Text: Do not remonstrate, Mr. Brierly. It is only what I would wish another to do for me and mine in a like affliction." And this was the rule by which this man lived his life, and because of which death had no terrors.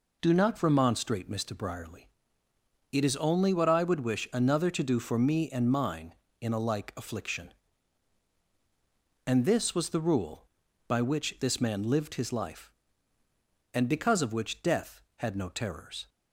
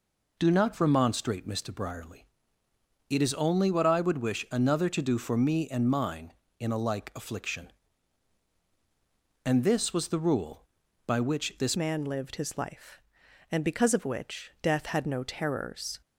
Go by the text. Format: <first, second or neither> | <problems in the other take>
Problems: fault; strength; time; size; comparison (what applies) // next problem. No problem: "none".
first | changes voice at "man"; from 11.7 s on; 4.3 s long